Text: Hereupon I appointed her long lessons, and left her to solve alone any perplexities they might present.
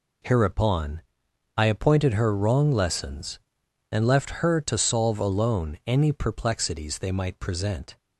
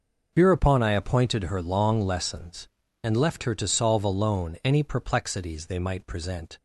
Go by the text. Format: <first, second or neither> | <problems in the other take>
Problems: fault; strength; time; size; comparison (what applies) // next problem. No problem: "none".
second | pauses between "Hereupon" and "I"; noticeable; at 1.0 s; 0.56 s long // says "wrong" for "long"; at 2.3 s